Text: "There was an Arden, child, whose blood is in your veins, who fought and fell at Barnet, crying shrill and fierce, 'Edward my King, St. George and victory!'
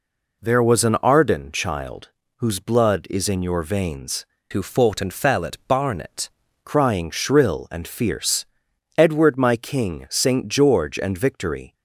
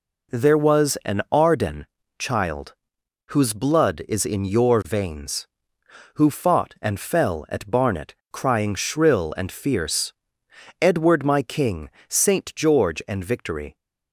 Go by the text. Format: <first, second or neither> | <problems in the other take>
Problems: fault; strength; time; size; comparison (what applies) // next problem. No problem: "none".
second | changes voice from "who" to "Barnet"; from 4.5 to 6.2 s; 1.7 s long